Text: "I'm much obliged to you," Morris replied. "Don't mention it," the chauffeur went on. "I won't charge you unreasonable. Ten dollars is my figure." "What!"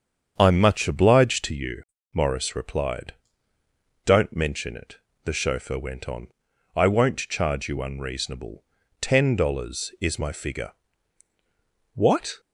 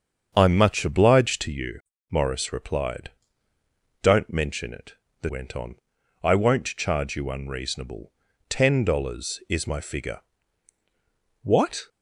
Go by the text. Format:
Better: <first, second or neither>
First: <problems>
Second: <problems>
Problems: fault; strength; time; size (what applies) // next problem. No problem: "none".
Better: first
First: starts louder than the rest; strong; until 1.3 s; 8 dB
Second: starts louder than the rest; strong; until 1.3 s; 7 dB // skips "chauffeur"; at 5.2 s